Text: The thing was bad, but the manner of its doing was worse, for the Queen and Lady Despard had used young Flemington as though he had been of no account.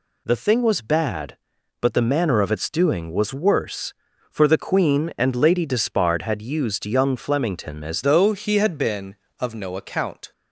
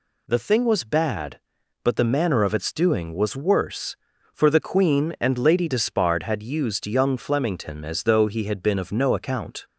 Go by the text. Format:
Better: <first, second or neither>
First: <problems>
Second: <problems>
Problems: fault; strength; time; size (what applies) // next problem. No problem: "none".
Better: second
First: changes voice at "though"; from 8.0 s on; 2.3 s long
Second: none